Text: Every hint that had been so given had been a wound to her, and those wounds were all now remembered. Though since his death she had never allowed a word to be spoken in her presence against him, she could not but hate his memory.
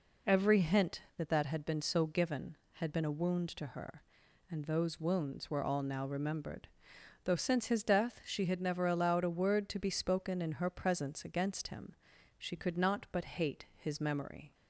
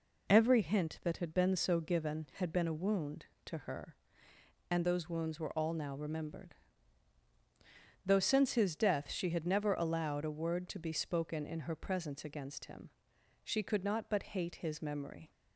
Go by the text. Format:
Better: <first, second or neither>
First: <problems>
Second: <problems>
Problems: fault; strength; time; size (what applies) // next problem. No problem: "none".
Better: second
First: says "that" twice; at 1.2 s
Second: none